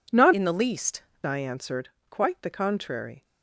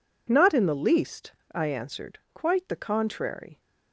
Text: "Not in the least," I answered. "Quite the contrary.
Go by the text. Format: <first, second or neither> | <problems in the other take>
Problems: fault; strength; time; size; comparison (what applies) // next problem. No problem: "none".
second | changes voice from "in" to "least"; from 0.3 to 1.0 s; 0.7 s long